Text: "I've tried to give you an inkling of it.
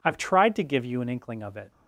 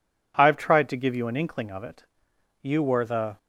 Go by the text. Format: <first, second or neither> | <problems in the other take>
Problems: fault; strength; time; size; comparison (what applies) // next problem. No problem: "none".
first | goes on to say "You were the"; noticeable; from 2.6 s on; 0.76 s long